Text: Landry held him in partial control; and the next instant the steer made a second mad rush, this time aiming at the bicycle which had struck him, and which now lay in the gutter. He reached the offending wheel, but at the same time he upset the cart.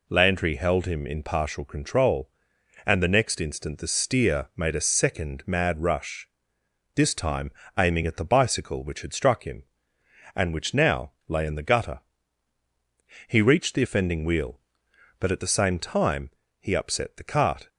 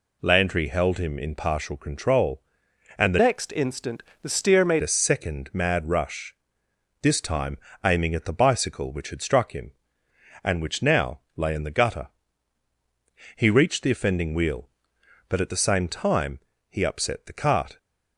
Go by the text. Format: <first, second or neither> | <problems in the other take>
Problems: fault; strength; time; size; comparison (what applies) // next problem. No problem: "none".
first | changes voice from "next" to "made"; from 3.1 to 4.8 s; 1.7 s long // pauses between "instant" and "the"; slight; at 4.0 s; 0.22 s long // pauses between "time" and "aiming"; slight; at 7.5 s; 0.24 s long; slight in the first // pauses between "now" and "lay"; slight; at 11.2 s; 0.16 s long; slight in the first // pauses between "time" and "he"; slight; at 16.3 s; 0.28 s long; slight in the first